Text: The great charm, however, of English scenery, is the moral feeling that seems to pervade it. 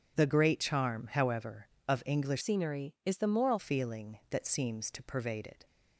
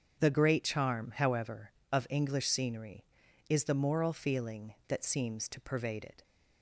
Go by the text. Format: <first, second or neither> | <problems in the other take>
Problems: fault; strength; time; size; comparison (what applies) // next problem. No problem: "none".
second | starts louder than the rest; strong; until 1.2 s; 7.5 dB; strong in the second // changes voice from "scenery" to "moral"; from 2.4 to 3.5 s; 1.1 s long